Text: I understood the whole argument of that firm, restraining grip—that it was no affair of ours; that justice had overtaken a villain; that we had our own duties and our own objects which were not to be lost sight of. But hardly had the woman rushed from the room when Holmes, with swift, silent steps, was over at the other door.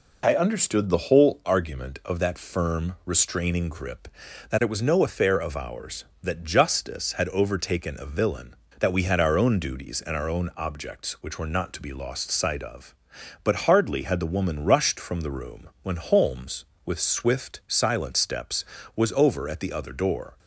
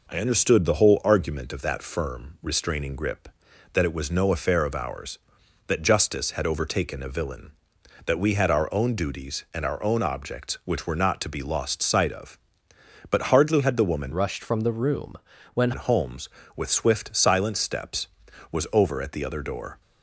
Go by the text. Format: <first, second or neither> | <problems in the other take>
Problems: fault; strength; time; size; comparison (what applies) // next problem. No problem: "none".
first | changes voice from "rushed" to "when"; from 14.1 to 15.7 s; 1.6 s long // pauses between "room" and "when"; at 15.1 s; 0.38 s long; slight in the first